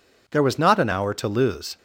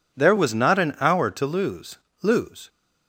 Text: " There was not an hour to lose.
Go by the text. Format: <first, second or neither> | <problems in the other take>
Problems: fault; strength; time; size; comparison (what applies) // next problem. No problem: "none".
first | says "lose" twice; at 2.2 s